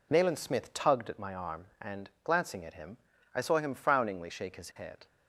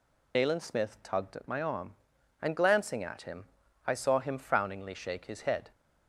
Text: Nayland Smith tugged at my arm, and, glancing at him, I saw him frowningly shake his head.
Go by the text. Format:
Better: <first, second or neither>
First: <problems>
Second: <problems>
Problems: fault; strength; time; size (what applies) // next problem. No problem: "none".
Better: first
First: none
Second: loses the start of "Nayland"; at 0.3 s; 45 ms